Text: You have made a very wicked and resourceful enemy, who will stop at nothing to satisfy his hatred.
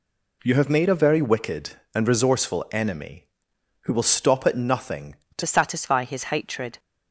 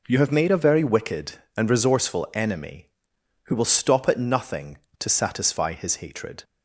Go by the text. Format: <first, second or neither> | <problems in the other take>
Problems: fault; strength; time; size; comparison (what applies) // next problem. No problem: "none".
second | changes voice at "satisfy"; from 5.4 s on; 1.3 s long